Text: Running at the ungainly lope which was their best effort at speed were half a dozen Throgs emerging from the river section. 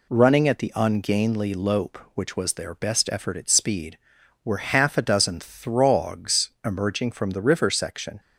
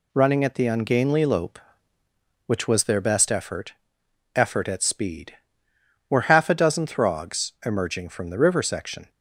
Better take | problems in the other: first | says "effort" twice; at 4.3 s

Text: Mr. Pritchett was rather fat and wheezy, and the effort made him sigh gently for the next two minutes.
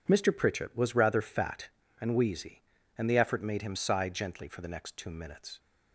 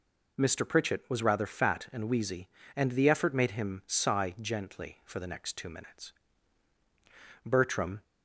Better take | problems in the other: first | goes on to say "Bertram"; from 7.4 s on; 0.58 s long

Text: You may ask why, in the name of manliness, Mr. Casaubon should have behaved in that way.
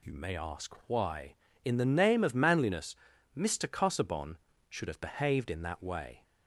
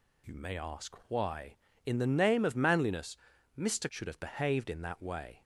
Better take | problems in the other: first | skips "Casaubon"; at 3.8 s

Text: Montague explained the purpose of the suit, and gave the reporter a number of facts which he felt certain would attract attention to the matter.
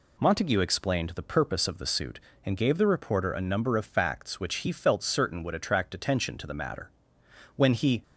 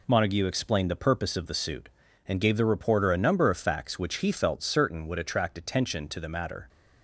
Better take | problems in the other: second | goes on to say "When he"; slight; from 7.5 s on; 0.46 s long

